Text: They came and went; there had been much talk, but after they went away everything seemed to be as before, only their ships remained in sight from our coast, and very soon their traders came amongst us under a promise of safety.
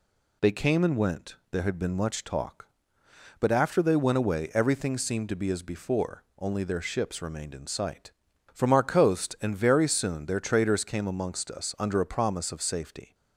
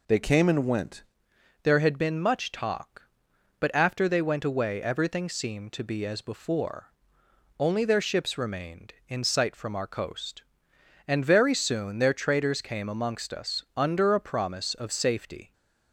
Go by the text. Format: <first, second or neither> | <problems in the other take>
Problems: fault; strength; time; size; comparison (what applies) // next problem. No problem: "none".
first | changes voice at "there"; from 1.6 s on; 13.9 s long